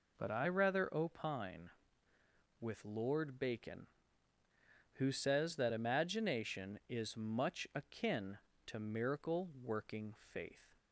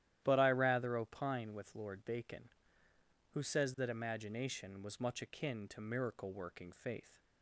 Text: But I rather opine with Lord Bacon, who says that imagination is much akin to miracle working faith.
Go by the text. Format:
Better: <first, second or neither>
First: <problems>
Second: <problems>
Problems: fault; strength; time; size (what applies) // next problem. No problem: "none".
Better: first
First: none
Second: starts louder than the rest; strong; until 1.2 s; 12 dB // says "was" for "is"; at 4.8 s